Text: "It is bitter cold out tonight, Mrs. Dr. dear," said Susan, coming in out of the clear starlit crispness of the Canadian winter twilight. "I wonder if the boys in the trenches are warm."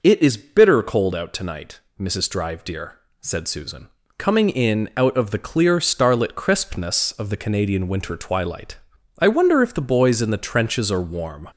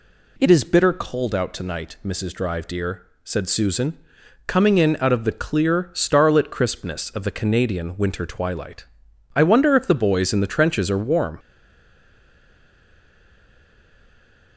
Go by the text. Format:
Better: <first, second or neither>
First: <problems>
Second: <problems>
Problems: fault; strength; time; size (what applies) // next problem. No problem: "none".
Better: first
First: none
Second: stays silent after the last word; strong; from 11.3 s on; 3.2 s long